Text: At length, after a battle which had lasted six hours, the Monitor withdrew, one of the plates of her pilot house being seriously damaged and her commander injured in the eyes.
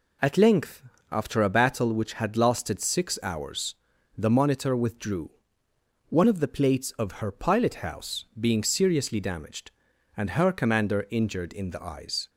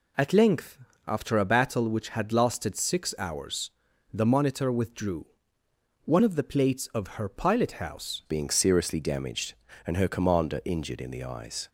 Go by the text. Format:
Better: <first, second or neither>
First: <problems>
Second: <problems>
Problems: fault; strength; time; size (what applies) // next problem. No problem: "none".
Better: first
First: none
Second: changes voice at "being"; from 8.2 s on; 3.4 s long